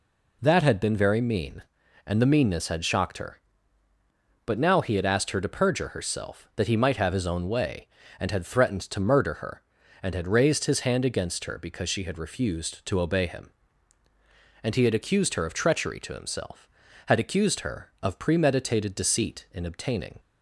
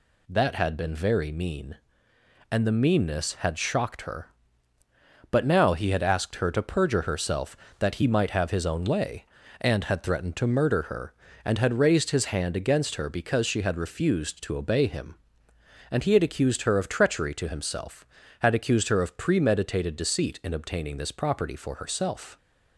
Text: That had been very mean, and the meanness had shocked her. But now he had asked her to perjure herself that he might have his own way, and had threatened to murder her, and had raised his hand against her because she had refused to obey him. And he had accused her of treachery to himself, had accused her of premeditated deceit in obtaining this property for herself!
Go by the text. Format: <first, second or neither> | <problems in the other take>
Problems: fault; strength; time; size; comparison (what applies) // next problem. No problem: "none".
second | stops before "this property for herself"; at 20.1 s